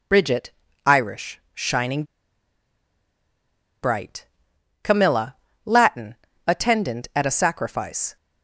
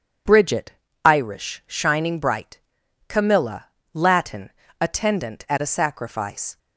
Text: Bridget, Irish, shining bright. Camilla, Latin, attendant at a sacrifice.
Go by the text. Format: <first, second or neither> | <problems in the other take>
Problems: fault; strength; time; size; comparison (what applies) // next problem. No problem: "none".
second | pauses between "shining" and "bright"; strong; at 2.0 s; 1.7 s long